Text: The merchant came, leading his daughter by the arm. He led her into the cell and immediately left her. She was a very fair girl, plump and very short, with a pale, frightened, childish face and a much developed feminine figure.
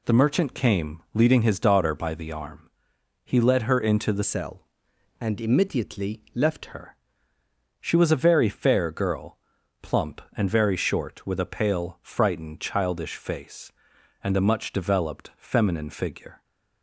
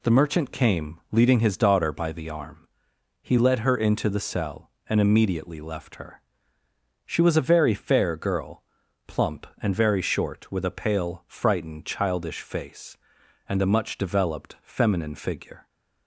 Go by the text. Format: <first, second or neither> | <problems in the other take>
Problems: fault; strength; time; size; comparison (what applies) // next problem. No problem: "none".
second | changes voice from "cell" to "left"; from 4.2 to 6.7 s; 2.5 s long